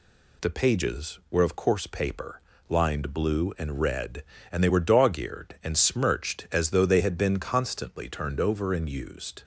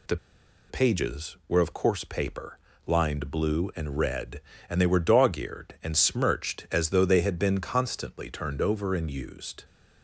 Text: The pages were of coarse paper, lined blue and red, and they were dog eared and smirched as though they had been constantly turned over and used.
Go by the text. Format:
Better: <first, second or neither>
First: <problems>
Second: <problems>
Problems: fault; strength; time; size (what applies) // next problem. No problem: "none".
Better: first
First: none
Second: pauses between "The" and "pages"; noticeable; at 0.1 s; 0.54 s long